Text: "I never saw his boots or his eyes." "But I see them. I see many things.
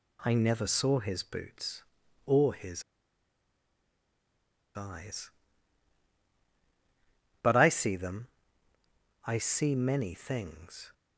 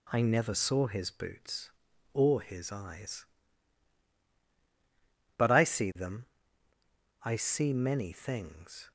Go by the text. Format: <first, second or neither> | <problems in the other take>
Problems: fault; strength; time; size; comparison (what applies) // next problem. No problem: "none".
second | pauses between "his" and "eyes"; strong; at 2.8 s; 1.9 s long